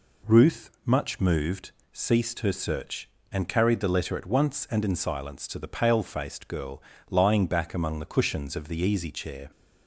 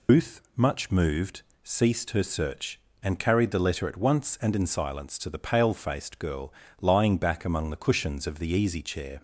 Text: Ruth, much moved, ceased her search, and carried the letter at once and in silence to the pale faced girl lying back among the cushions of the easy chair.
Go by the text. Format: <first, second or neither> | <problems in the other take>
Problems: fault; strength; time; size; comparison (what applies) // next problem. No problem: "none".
first | loses the start of "Ruth"; at 0.0 s; 150 ms // pauses between "girl" and "lying"; slight; at 6.5 s; 0.28 s long; slight in the first